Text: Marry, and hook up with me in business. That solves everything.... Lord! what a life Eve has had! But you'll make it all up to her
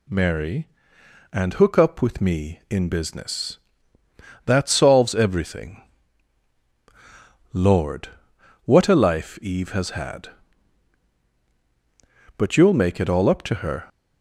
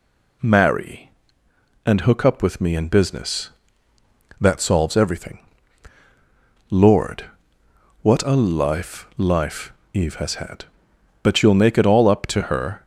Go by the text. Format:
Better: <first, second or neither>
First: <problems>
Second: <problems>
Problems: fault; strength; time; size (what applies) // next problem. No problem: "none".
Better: first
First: none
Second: says "life" twice; at 9.1 s